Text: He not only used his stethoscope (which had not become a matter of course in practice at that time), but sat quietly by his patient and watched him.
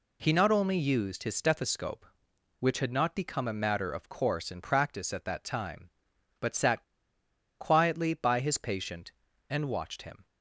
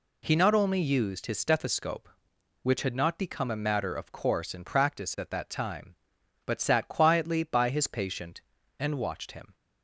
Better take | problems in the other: second | pauses between "sat" and "quietly"; noticeable; at 6.8 s; 0.77 s long

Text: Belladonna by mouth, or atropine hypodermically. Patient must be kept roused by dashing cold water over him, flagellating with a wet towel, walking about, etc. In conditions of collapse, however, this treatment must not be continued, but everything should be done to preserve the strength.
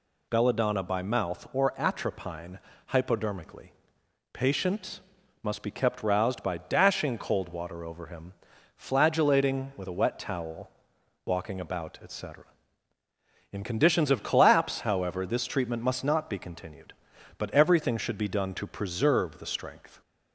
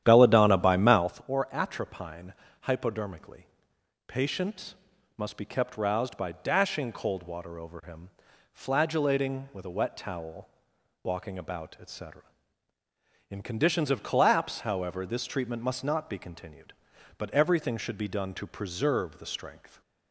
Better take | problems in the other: first | starts louder than the rest; strong; until 1.2 s; 10.5 dB // pauses between "atropine" and "hypodermically"; slight; at 2.3 s; 0.28 s long; slight in the first // pauses between "Patient" and "must"; at 4.7 s; 0.42 s long; also in the first

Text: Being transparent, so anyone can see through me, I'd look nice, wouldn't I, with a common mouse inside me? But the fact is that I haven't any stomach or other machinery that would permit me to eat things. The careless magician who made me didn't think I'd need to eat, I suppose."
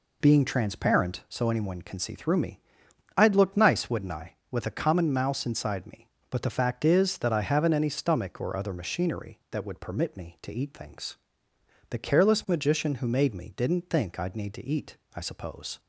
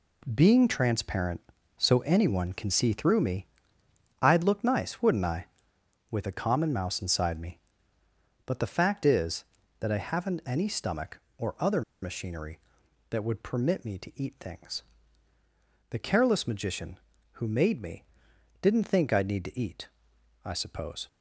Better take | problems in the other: first | pauses between "other" and "machinery"; slight; at 11.8 s; 0.21 s long // pauses between "me" and "didn't"; noticeable; at 18.0 s; 0.60 s long

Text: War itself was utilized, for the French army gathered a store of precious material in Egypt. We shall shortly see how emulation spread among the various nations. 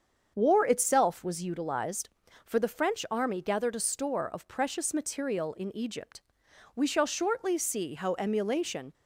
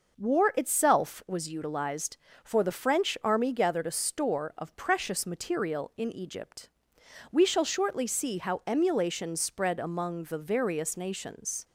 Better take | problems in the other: second | starts louder than the rest; strong; until 1.3 s; 7 dB // stops before "spread among the various nations"; at 8.9 s

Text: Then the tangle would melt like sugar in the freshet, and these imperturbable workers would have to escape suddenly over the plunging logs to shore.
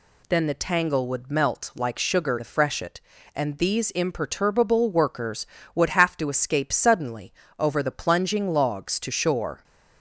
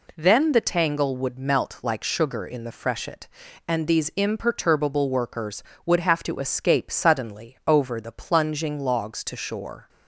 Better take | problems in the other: second | skips "in"; at 2.3 s // pauses between "suddenly" and "over"; slight; at 7.3 s; 0.24 s long

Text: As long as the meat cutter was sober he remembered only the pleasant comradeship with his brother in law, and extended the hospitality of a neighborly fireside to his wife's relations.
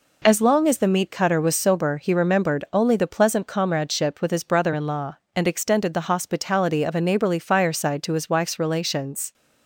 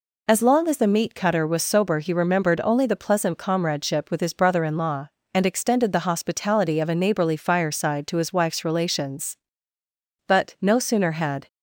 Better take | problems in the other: first | goes on to say "But no sooner had"; noticeable; from 10.2 s on; 1.2 s long

